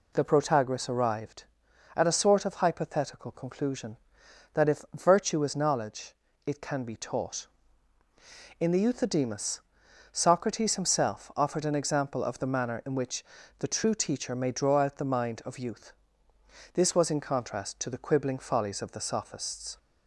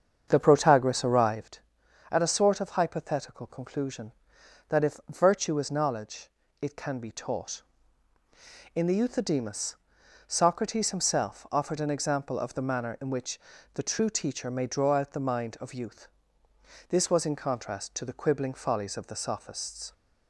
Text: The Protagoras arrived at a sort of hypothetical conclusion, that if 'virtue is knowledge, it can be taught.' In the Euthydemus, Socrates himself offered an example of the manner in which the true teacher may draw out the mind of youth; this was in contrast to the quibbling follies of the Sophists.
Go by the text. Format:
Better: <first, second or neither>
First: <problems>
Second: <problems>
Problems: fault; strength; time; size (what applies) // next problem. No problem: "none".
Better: first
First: pauses between "which" and "the"; slight; at 13.2 s; 0.34 s long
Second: starts louder than the rest; strong; until 1.5 s; 7.5 dB // pauses between "which" and "the"; slight; at 13.3 s; 0.34 s long